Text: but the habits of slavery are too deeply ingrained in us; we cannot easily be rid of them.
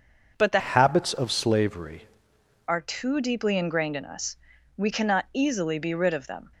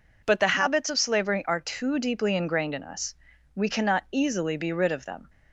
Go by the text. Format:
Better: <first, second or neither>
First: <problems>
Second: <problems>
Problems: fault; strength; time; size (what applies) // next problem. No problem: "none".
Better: second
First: starts louder than the rest; until 1.3 s; 6 dB // changes voice from "habits" to "slavery"; from 0.5 to 2.0 s; 1.5 s long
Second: none